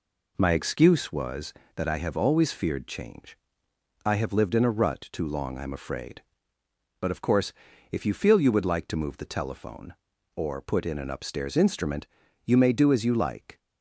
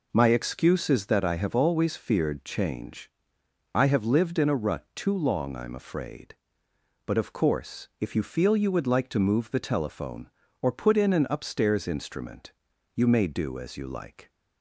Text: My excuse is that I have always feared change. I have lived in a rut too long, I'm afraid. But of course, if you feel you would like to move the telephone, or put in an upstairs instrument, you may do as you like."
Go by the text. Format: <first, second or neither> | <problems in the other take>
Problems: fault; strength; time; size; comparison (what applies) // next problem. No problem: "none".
second | says "was" for "is"; at 1.1 s